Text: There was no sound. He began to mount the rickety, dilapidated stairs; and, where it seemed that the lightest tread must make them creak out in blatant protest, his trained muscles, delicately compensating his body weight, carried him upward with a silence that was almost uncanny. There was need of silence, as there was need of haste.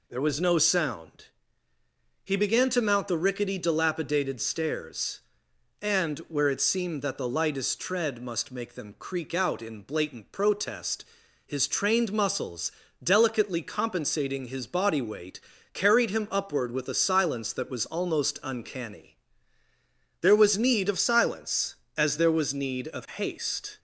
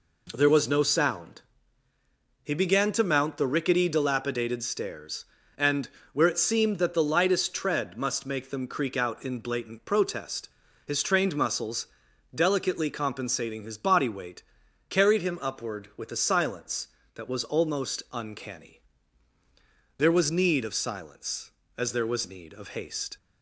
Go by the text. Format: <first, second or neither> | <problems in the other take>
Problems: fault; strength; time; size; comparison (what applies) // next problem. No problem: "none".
neither | none